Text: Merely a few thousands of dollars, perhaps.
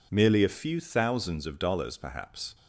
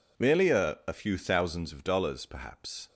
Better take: first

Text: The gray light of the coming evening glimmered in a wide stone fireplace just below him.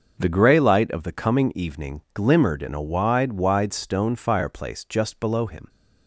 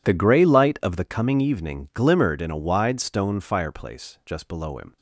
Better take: second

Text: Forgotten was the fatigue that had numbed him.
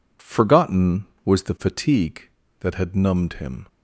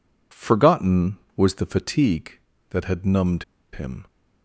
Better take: first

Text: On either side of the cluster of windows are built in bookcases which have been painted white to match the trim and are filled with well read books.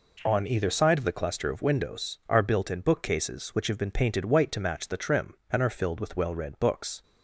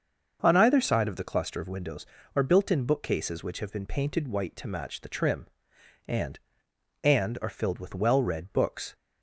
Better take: first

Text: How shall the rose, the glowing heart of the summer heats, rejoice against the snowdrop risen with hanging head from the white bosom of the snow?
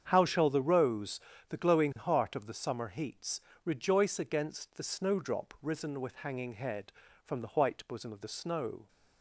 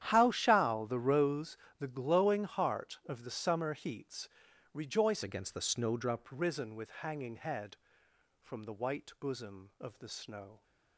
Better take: first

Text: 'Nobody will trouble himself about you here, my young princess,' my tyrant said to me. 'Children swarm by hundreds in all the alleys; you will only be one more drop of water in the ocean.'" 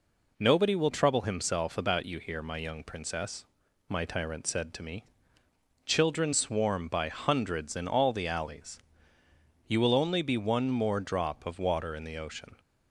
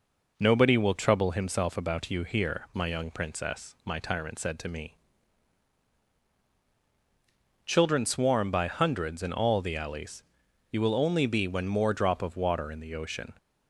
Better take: first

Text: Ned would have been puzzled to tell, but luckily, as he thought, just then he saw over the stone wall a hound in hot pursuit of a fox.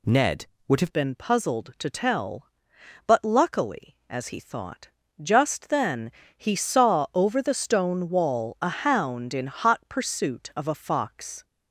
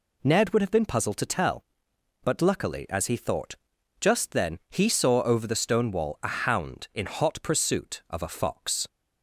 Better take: second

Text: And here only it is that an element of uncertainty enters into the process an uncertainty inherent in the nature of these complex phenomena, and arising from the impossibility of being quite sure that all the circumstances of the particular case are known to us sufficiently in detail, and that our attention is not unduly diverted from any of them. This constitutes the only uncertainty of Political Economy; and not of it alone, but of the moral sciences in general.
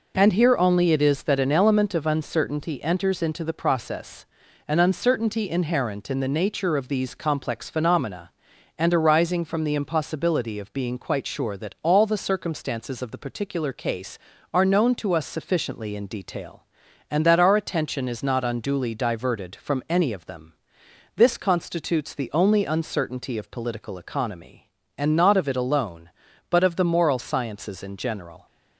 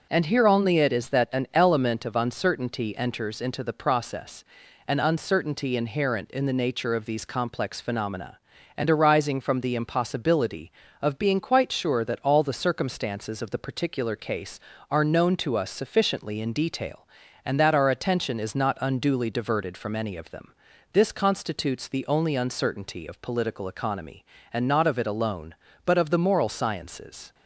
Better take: first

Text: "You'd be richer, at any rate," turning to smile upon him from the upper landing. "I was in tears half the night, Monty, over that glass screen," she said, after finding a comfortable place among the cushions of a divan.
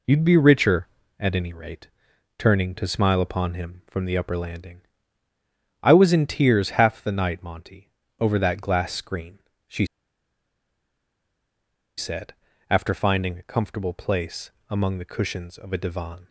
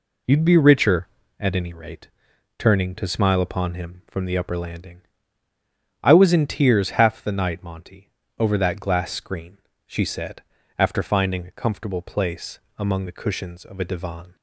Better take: second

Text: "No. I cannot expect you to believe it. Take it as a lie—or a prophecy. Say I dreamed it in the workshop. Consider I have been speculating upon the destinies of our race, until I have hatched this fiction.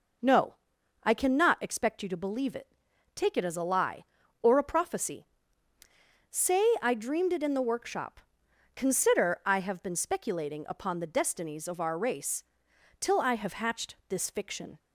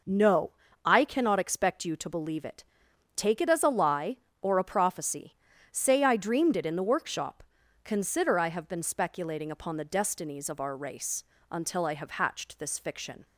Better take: second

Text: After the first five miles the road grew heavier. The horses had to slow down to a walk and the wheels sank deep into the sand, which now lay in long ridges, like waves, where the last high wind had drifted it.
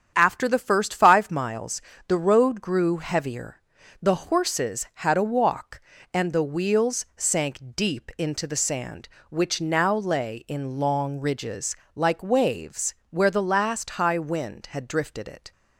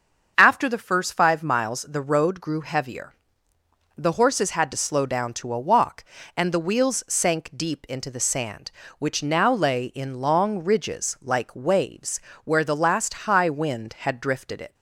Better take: second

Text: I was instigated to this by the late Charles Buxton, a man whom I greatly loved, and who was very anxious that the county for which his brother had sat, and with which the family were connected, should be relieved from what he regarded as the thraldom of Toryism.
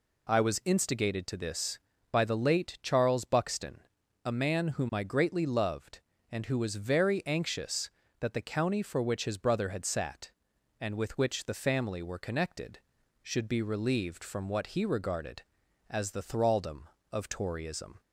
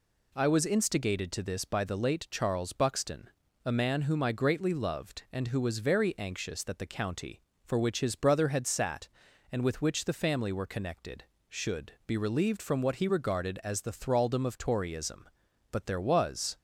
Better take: first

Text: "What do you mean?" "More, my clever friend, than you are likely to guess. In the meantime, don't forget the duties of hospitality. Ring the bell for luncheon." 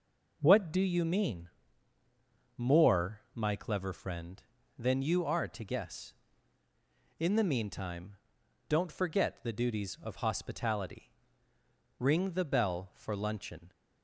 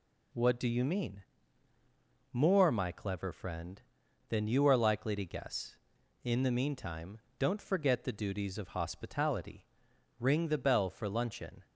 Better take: second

